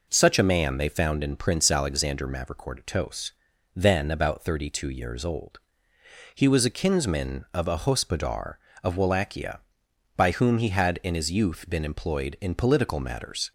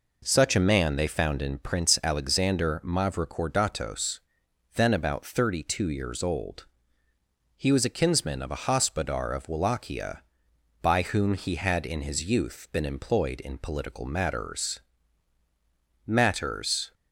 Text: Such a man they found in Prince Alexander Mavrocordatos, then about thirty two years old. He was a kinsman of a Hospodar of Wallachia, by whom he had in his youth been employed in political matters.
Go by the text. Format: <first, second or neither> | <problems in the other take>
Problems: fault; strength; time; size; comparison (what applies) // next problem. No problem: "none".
first | says "matters" twice; at 16.0 s